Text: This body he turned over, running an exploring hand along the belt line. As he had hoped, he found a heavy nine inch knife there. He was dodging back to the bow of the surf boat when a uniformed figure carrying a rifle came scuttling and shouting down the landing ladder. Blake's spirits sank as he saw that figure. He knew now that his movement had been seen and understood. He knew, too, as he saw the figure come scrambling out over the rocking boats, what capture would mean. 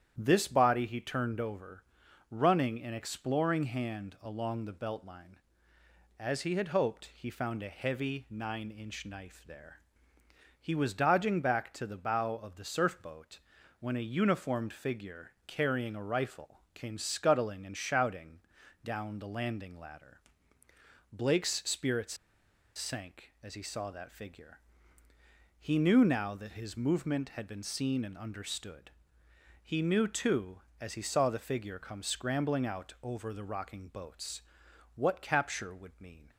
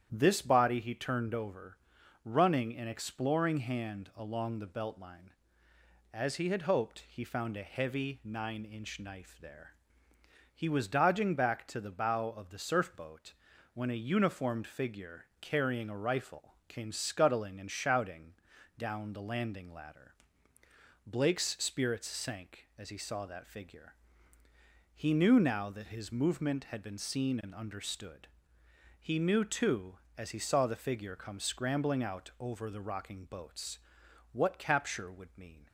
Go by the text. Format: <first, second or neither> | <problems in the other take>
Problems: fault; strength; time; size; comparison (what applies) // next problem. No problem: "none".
second | starts louder than the rest; strong; until 1.1 s; 9.5 dB; strong in the second // pauses between "boat" and "when"; at 13.3 s; 0.40 s long; also in the second // pauses between "shouting" and "down"; at 18.3 s; 0.44 s long; also in the second // pauses between "spirits" and "sank"; noticeable; at 22.1 s; 0.60 s long